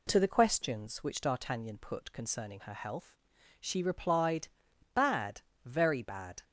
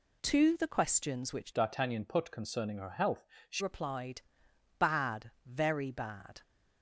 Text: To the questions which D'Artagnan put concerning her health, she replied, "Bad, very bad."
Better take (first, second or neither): first